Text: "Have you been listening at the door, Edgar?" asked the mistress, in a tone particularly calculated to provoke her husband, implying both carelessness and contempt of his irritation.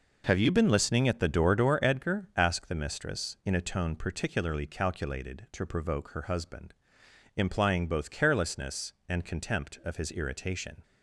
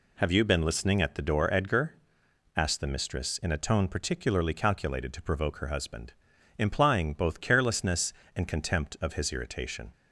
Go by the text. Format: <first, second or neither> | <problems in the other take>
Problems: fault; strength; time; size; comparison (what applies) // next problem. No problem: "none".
second | says "door" twice; at 1.5 s